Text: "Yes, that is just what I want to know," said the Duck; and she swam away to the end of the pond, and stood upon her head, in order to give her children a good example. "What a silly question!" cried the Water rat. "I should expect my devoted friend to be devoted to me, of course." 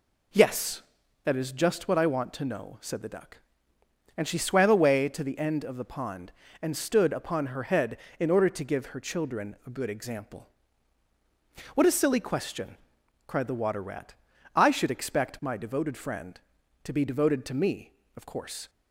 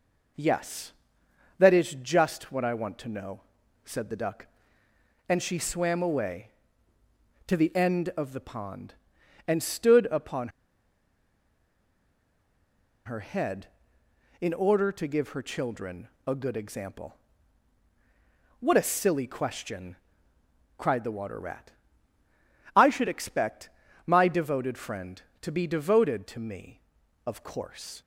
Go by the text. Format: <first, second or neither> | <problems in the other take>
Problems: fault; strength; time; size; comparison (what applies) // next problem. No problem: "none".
first | pauses between "upon" and "her"; strong; at 10.4 s; 2.5 s long // pauses between "children" and "a"; slight; at 16.0 s; 0.18 s long // pauses between "expect" and "my"; at 23.6 s; 0.38 s long